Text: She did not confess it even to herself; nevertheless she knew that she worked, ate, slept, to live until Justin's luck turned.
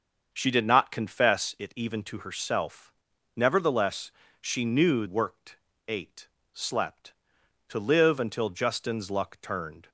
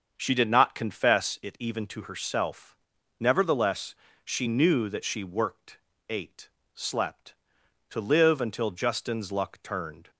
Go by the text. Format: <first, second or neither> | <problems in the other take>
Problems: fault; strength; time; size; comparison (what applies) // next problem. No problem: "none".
second | starts louder than the rest; until 1.3 s; 6.5 dB; also in the second // pauses between "nevertheless" and "she"; slight; at 4.1 s; 0.28 s long; slight in the second // skips "that she"; at 5.0 s